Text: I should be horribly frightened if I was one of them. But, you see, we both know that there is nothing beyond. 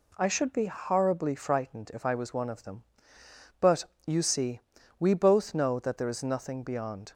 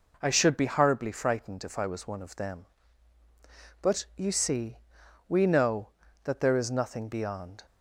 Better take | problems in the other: first | skips "both"; at 5.4 s

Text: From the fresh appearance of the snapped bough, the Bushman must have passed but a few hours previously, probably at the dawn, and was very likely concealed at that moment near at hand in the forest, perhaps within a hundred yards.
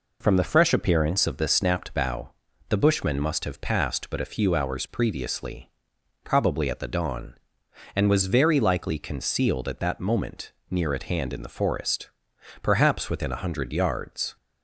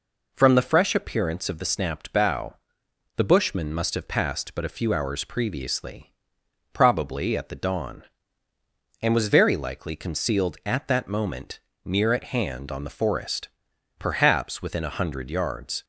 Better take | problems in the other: first | pauses between "moment" and "near"; slight; at 11.5 s; 0.24 s long; slight in the first // says "on" for "in"; at 12.6 s

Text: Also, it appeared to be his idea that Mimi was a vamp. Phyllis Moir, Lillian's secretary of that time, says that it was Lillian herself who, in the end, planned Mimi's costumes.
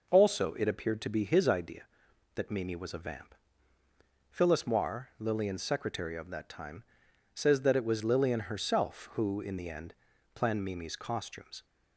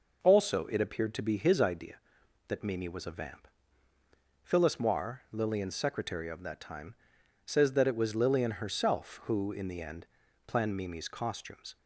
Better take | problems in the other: neither | none

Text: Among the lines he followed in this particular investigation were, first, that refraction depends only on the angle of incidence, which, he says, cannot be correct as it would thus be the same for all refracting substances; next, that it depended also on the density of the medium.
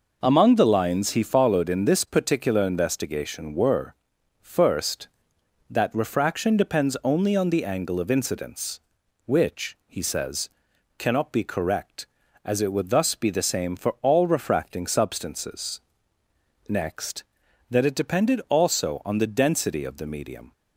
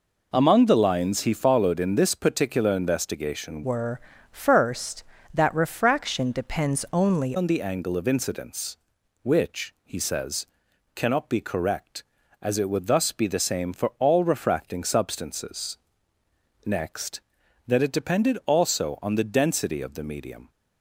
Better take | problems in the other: first | changes voice from "were" to "only"; from 3.6 to 7.3 s; 3.7 s long

